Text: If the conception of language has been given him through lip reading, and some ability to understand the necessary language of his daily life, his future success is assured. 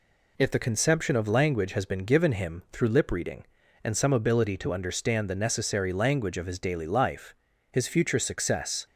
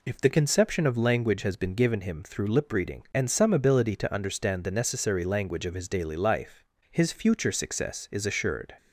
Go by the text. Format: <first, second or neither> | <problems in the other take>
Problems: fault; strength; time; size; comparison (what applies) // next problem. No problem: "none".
second | stops before "is assured"; at 8.8 s